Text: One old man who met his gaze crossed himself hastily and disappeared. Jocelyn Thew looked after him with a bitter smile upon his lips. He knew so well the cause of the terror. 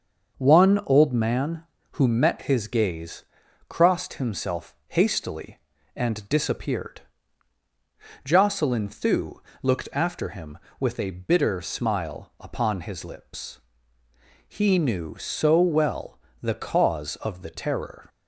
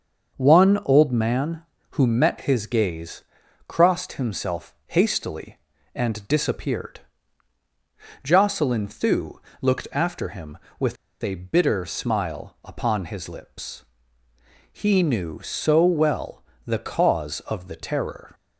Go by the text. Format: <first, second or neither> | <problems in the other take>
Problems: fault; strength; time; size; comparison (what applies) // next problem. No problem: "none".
first | starts louder than the rest; until 1.4 s; 6.5 dB; also in the first // pauses between "gaze" and "crossed"; noticeable; at 3.2 s; 0.46 s long; noticeable in the first // pauses between "Thew" and "looked"; slight; at 9.3 s; 0.22 s long; slight in the first // pauses between "with" and "a"; slight; at 10.9 s; 0.26 s long // pauses between "well" and "the"; slight; at 16.4 s; 0.24 s long; slight in the first